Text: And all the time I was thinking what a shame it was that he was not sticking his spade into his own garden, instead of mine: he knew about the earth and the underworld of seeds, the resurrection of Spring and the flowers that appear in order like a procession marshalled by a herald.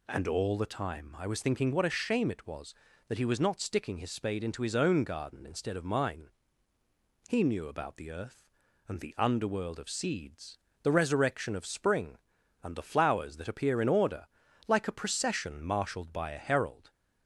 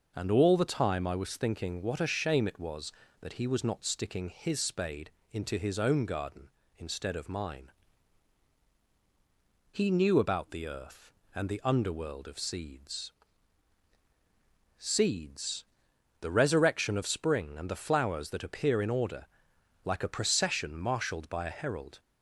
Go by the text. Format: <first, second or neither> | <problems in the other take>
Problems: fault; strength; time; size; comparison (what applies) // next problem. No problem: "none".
first | starts louder than the rest; noticeable; until 1.1 s; 6 dB // pauses between "spade" and "into"; slight; at 5.0 s; 0.22 s long // says "seeds" twice; at 14.7 s // pauses between "order" and "like"; noticeable; at 19.2 s; 0.56 s long; also in the first